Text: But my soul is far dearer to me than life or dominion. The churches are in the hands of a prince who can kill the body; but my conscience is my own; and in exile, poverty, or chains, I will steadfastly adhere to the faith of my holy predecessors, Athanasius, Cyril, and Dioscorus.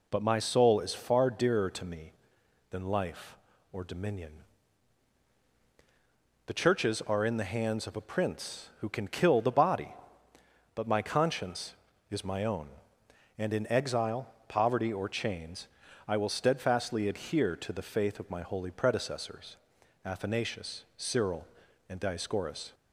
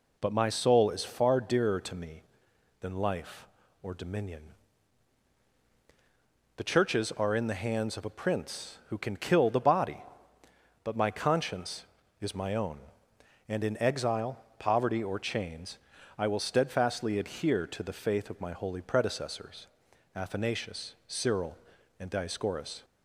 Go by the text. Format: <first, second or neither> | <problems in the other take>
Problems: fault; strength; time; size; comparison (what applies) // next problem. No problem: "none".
neither | none